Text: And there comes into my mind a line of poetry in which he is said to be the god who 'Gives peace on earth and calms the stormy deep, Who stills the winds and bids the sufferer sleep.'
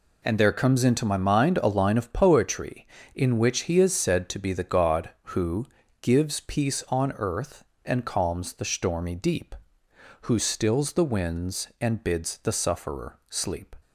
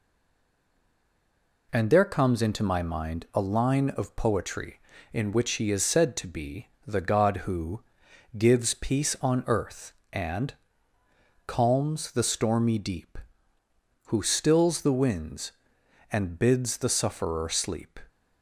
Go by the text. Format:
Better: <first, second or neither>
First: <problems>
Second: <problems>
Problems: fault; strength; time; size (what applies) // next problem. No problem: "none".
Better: first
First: pauses between "who" and "Gives"; slight; at 5.6 s; 0.36 s long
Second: stays silent before the first word; noticeable; until 1.6 s; 1.6 s long // pauses between "be" and "the"; slight; at 6.6 s; 0.18 s long // pauses between "who" and "Gives"; noticeable; at 7.8 s; 0.56 s long // pauses between "and" and "calms"; noticeable; at 10.5 s; 0.94 s long